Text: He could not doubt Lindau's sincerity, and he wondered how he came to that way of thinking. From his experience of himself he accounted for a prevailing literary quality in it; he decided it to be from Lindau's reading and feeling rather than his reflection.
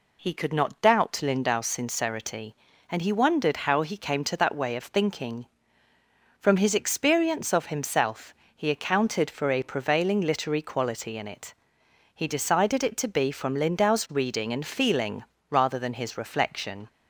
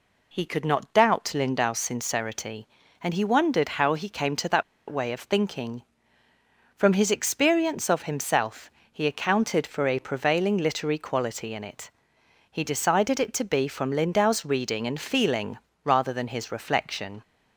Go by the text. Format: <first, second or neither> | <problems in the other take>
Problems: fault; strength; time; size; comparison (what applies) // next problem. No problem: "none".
first | pauses between "that" and "way"; slight; at 4.6 s; 0.26 s long // pauses between "himself" and "he"; slight; at 8.6 s; 0.20 s long; slight in the first // pauses between "feeling" and "rather"; slight; at 15.5 s; 0.26 s long; slight in the first